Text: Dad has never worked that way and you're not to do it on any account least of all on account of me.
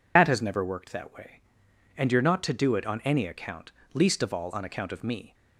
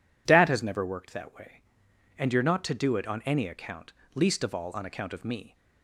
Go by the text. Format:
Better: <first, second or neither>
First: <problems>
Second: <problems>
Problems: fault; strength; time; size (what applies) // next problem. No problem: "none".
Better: second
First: loses the start of "Dad"; at 0.1 s; 100 ms // pauses between "account" and "least"; slight; at 3.7 s; 0.22 s long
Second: pauses between "account" and "least"; slight; at 3.9 s; 0.22 s long